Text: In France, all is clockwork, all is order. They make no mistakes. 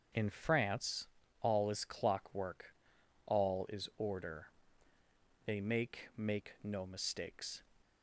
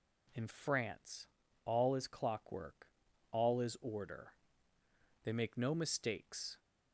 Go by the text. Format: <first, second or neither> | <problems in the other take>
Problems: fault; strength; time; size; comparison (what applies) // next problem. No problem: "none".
second | starts louder than the rest; until 1.4 s; 7 dB // says "make" twice; at 6.1 s